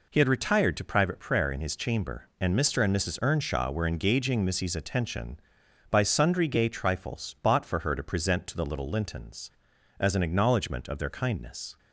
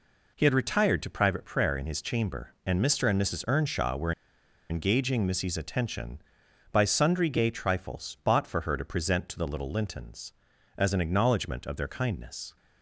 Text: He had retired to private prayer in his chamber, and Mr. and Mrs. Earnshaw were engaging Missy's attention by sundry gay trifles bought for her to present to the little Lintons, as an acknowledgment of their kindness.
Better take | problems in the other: first | pauses between "were" and "engaging"; noticeable; at 4.1 s; 0.58 s long

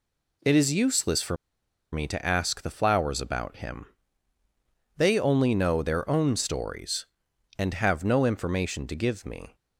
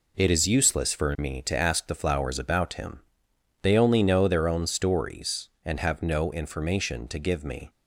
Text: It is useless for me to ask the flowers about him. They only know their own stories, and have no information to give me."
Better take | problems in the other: second | pauses between "for" and "me"; noticeable; at 1.3 s; 0.57 s long

